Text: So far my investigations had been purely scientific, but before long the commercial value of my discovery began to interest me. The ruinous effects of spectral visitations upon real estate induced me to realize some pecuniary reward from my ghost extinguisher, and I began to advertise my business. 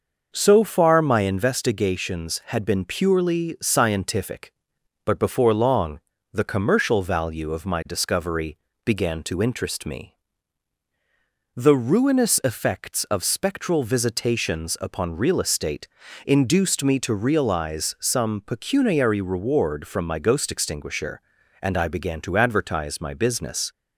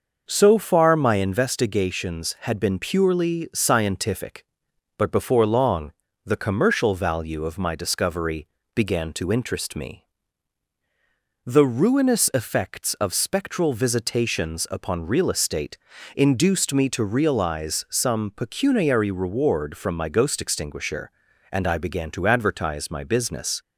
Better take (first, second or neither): neither